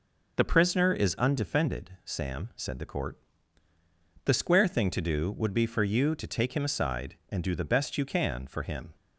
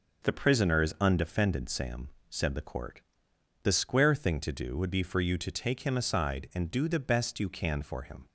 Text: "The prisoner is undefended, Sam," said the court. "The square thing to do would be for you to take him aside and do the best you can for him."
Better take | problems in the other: neither | none

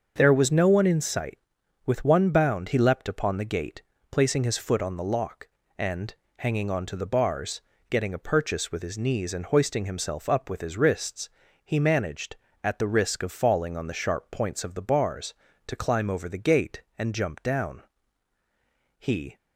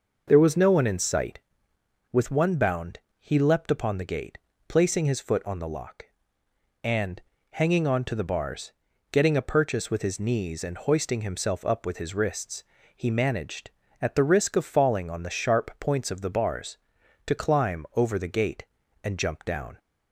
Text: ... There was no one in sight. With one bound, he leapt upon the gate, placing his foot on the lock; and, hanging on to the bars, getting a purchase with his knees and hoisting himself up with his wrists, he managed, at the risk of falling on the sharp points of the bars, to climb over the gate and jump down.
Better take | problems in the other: second | starts louder than the rest; until 1.1 s; 6.5 dB // goes on to say "He"; slight; from 18.9 s on; 0.38 s long

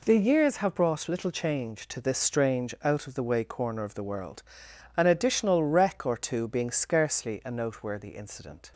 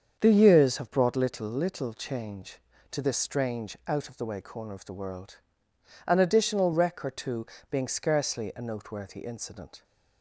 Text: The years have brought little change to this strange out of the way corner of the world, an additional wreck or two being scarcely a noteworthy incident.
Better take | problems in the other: first | starts louder than the rest; strong; until 1.2 s; 7 dB // says "little" twice; at 1.4 s // pauses between "two" and "being"; slight; at 7.4 s; 0.24 s long

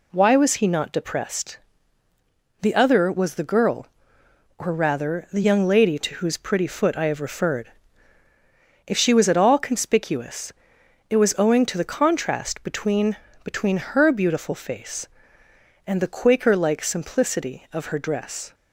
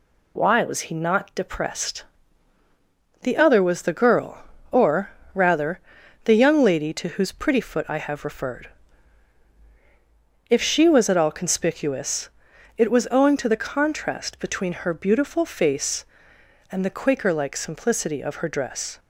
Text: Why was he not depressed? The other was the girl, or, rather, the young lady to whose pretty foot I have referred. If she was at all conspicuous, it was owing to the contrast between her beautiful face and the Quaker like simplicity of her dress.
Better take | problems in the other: second | says "between" twice; at 13.4 s

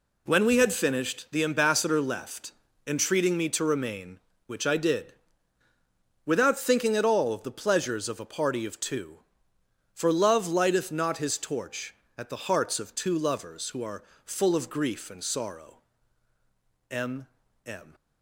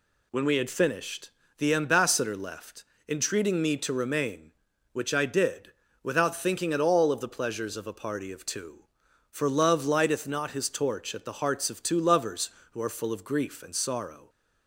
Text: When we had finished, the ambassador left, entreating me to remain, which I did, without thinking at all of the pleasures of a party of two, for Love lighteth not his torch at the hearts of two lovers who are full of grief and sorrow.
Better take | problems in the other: second | pauses between "are" and "full"; slight; at 14.0 s; 0.22 s long // goes on to say "M M"; noticeable; from 16.9 s on; 1.0 s long

